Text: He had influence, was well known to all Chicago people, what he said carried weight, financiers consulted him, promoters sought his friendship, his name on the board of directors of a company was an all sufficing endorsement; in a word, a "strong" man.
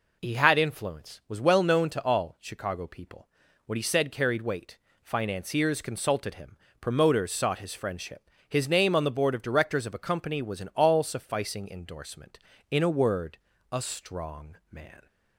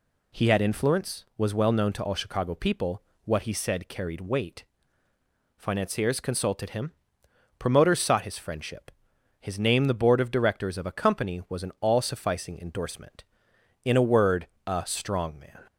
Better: first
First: none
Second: skips "on"; at 9.8 s

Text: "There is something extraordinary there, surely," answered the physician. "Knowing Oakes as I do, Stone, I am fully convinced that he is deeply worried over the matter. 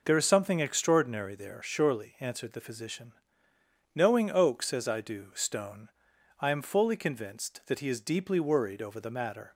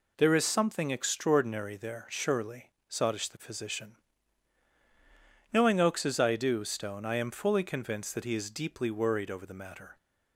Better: first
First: none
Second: says "sottish" for "answered"; at 2.8 s

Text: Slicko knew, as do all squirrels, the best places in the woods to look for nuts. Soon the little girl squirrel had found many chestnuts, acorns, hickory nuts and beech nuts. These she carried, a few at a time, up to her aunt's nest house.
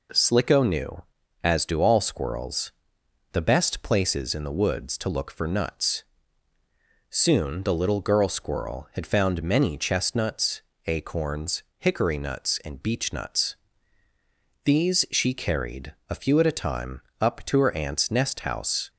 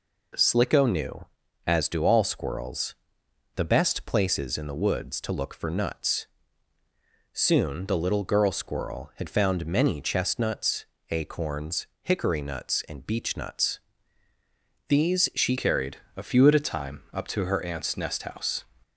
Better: first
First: none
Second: changes voice at "carried"; from 15.5 s on; 3.1 s long

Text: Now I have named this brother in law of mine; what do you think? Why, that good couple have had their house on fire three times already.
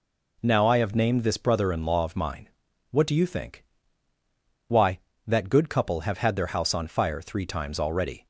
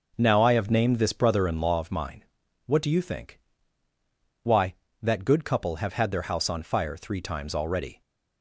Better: first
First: none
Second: starts louder than the rest; noticeable; until 1.8 s; 6 dB

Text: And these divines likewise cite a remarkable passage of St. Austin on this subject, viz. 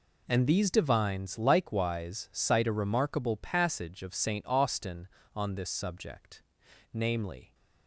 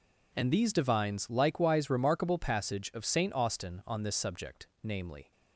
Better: first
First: none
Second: skips "cite a"; at 1.8 s

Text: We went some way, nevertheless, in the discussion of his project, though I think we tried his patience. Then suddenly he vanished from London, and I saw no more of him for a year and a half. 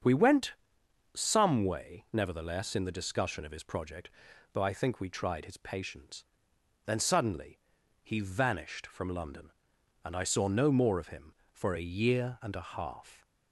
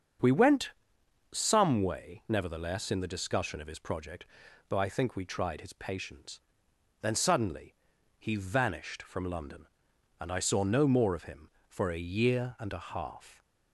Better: neither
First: starts louder than the rest; strong; until 1.6 s; 7 dB // pauses between "went" and "some"; noticeable; at 0.5 s; 0.62 s long // pauses between "suddenly" and "he"; at 7.5 s; 0.44 s long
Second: starts louder than the rest; strong; until 1.8 s; 7 dB // pauses between "went" and "some"; noticeable; at 0.7 s; 0.62 s long // pauses between "suddenly" and "he"; at 7.7 s; 0.44 s long

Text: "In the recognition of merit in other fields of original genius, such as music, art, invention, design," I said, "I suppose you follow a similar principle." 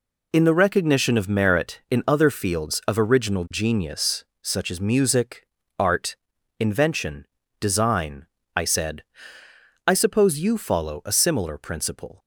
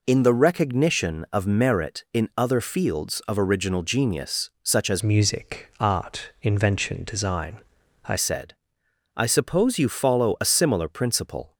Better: first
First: none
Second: changes voice from "music" to "I"; from 5.0 to 8.1 s; 3.1 s long

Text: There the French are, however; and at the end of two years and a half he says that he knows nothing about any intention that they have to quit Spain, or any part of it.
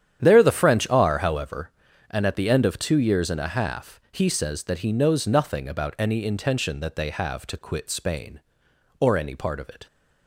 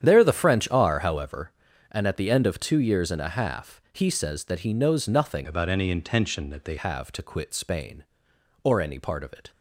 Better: first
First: starts louder than the rest; strong; until 1.2 s; 9.5 dB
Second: starts louder than the rest; strong; until 1.0 s; 9.5 dB // changes voice from "about" to "they"; from 5.4 to 6.7 s; 1.3 s long

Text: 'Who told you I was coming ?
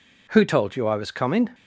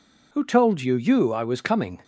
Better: first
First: none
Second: says "you" twice; at 0.9 s

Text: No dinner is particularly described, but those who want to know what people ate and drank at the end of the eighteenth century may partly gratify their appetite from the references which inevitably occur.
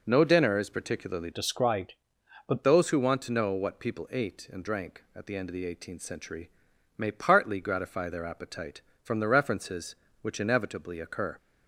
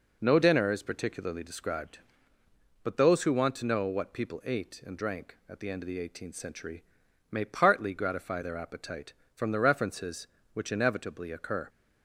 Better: second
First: changes voice from "described" to "but"; from 1.3 to 2.6 s; 1.3 s long // pauses between "century" and "may"; noticeable; at 6.4 s; 0.48 s long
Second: pauses between "century" and "may"; noticeable; at 6.8 s; 0.48 s long

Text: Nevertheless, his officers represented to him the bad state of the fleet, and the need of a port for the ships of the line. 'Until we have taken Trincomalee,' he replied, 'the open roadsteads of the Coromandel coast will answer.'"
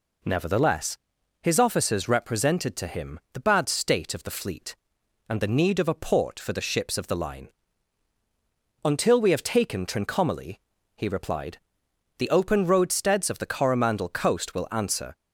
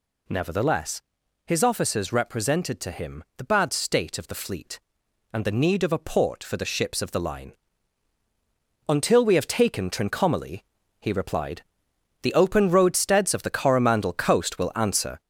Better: first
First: none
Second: gets louder; noticeable; throughout; 5 dB

